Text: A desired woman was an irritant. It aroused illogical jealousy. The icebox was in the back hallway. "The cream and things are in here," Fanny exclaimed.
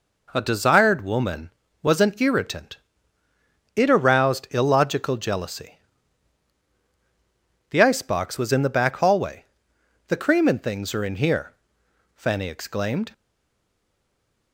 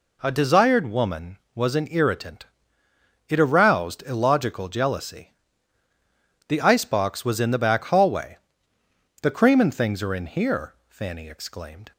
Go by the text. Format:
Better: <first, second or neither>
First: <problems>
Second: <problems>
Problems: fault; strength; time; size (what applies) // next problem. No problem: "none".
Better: second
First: stays silent after the last word; noticeable; from 13.1 s on; 1.4 s long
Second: none